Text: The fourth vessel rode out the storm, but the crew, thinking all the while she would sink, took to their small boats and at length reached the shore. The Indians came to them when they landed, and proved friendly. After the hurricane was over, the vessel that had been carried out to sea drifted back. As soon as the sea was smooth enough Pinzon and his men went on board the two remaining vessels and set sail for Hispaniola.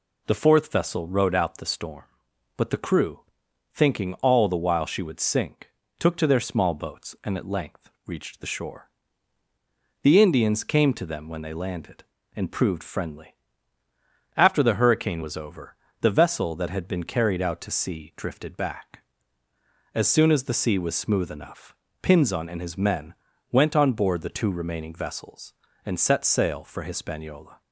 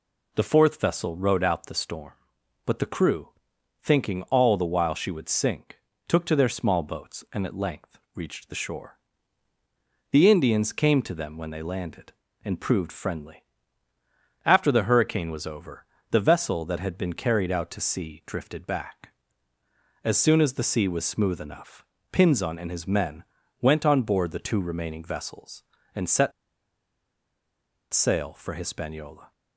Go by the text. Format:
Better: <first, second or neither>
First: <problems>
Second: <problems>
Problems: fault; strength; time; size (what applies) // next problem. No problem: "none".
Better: first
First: pauses between "length" and "reached"; slight; at 7.8 s; 0.16 s long // pauses between "enough" and "Pinzon"; slight; at 21.7 s; 0.26 s long // pauses between "men" and "went"; slight; at 23.1 s; 0.36 s long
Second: pauses between "length" and "reached"; slight; at 7.9 s; 0.16 s long // pauses between "enough" and "Pinzon"; slight; at 21.8 s; 0.26 s long // pauses between "men" and "went"; slight; at 23.2 s; 0.36 s long // pauses between "set" and "sail"; strong; at 26.3 s; 1.6 s long